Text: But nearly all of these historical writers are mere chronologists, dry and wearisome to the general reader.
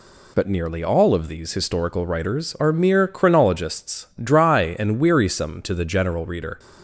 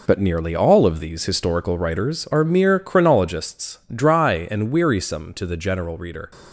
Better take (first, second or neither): first